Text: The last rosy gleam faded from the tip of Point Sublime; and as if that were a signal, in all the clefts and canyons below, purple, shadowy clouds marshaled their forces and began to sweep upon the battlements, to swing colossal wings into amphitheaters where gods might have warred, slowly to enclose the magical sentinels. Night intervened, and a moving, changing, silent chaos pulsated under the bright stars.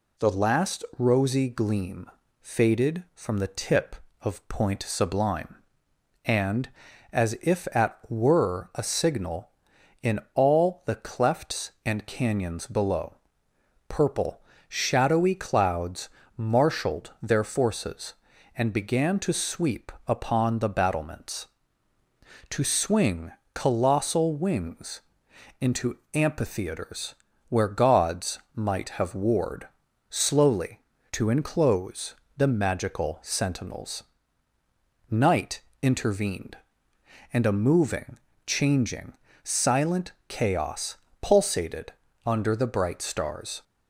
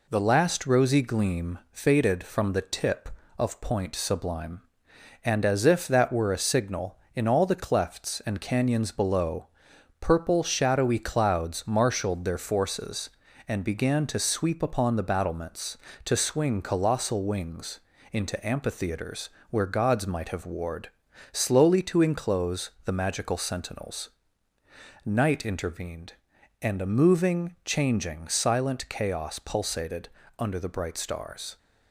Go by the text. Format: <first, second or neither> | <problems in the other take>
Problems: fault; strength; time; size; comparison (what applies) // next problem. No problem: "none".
second | pauses between "gleam" and "faded"; slight; at 2.0 s; 0.32 s long // says "at" for "that"; at 7.7 s // pauses between "clouds" and "marshaled"; slight; at 16.0 s; 0.26 s long // pauses between "sweep" and "upon"; slight; at 19.9 s; 0.16 s long // pauses between "swing" and "colossal"; slight; at 23.3 s; 0.22 s long // pauses between "wings" and "into"; noticeable; at 25.0 s; 0.60 s long; slight in the second // pauses between "into" and "amphitheaters"; slight; at 25.9 s; 0.18 s long // pauses between "amphitheaters" and "where"; slight; at 27.1 s; 0.36 s long; slight in the second // pauses between "gods" and "might"; slight; at 28.3 s; 0.16 s long // pauses between "enclose" and "the"; slight; at 32.1 s; 0.24 s long // pauses between "Night" and "intervened"; slight; at 35.6 s; 0.20 s long // pauses between "silent" and "chaos"; slight; at 40.1 s; 0.16 s long // pauses between "chaos" and "pulsated"; slight; at 40.9 s; 0.26 s long // pauses between "pulsated" and "under"; slight; at 41.8 s; 0.36 s long; slight in the second